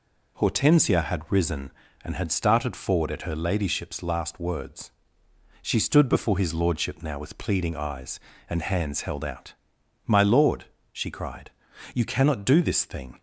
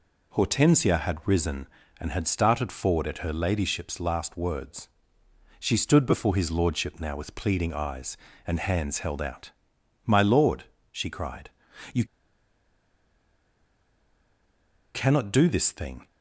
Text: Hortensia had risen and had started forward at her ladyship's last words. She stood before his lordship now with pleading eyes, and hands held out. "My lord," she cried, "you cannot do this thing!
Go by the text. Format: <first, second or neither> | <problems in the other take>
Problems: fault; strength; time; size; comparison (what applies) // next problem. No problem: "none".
first | pauses between "you" and "cannot"; strong; at 12.0 s; 2.9 s long